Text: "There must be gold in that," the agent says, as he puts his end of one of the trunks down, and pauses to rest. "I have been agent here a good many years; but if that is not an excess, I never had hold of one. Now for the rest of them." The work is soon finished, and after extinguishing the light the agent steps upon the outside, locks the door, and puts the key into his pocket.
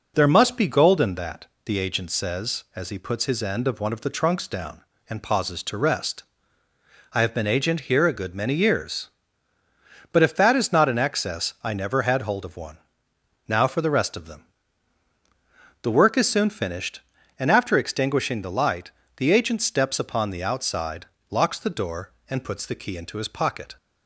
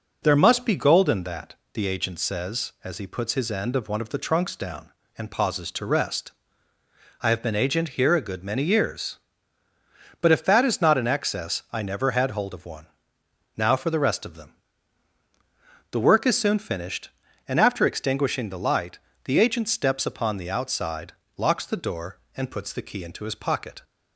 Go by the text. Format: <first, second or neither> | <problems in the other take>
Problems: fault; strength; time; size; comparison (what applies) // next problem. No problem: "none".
neither | pauses between "light" and "the"; slight; the same in both